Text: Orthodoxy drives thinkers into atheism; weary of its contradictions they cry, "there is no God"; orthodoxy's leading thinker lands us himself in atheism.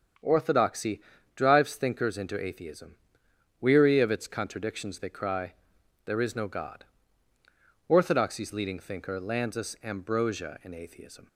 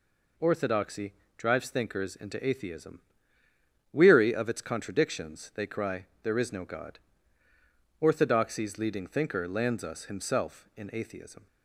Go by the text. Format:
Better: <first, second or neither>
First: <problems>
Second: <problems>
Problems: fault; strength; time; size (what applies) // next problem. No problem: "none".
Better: second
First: starts louder than the rest; strong; until 1.5 s; 7.5 dB // pauses between "Orthodoxy" and "drives"; slight; at 1.0 s; 0.34 s long // says "ambrosia" for "himself"; at 9.8 s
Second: pauses between "Orthodoxy" and "drives"; slight; at 1.1 s; 0.24 s long